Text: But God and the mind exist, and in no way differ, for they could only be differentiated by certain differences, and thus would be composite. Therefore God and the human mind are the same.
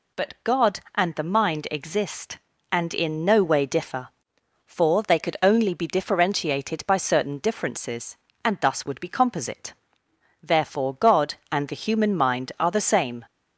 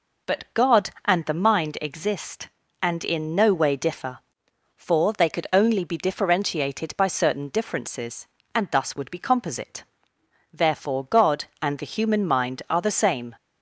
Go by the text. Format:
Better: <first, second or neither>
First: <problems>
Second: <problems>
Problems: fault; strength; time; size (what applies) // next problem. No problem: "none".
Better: first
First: none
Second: starts louder than the rest; noticeable; until 1.7 s; 5 dB